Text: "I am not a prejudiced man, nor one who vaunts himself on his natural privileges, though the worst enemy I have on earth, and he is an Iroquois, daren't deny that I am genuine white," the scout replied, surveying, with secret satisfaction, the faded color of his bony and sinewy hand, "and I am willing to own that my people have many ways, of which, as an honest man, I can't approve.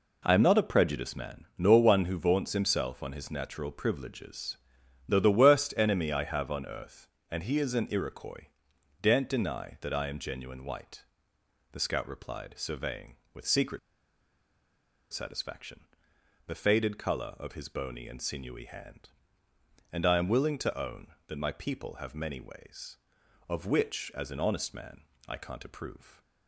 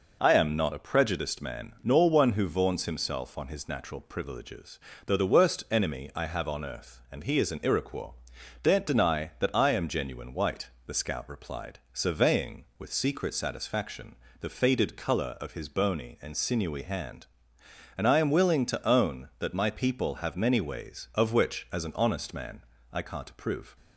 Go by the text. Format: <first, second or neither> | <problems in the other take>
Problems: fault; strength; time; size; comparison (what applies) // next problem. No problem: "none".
second | pauses between "secret" and "satisfaction"; strong; at 13.7 s; 1.3 s long